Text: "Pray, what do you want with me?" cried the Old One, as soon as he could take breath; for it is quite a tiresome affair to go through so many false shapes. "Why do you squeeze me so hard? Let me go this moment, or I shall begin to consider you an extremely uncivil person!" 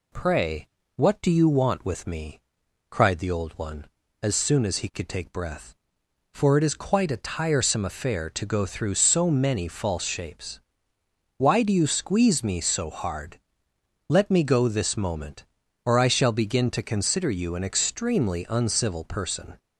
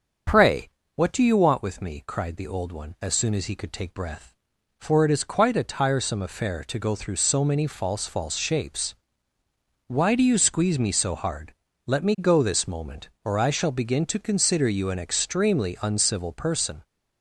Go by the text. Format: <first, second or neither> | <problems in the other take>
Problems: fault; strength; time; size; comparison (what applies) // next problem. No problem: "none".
first | starts louder than the rest; strong; until 1.5 s; 7 dB // says "false" twice; at 8.0 s